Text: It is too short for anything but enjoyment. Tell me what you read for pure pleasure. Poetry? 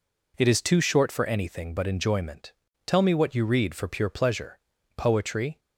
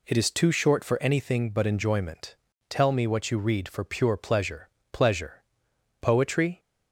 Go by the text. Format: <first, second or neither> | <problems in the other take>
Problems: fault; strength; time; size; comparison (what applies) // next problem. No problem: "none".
first | says "pleasure" twice; at 4.9 s